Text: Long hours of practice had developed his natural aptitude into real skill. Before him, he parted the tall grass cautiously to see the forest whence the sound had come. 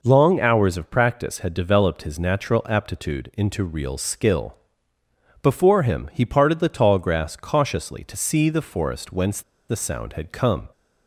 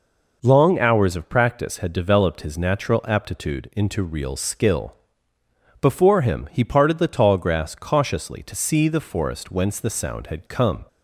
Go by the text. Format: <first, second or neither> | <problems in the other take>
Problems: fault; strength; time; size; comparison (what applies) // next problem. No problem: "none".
second | pauses between "whence" and "the"; slight; at 9.4 s; 0.27 s long